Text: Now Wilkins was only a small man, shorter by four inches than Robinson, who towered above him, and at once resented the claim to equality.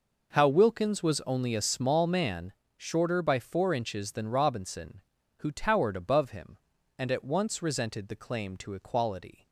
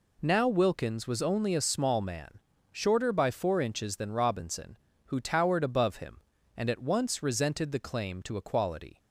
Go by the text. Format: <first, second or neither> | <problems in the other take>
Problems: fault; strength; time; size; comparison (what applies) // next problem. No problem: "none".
second | says "How" for "Now"; at 0.3 s